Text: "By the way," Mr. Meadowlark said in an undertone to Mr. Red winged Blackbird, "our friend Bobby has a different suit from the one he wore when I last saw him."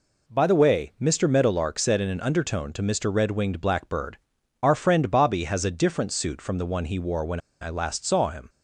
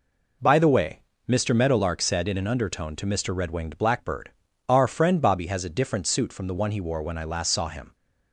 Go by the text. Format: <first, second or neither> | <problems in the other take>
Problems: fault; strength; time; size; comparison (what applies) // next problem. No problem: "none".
second | pauses between "when" and "I"; slight; at 7.3 s; 0.22 s long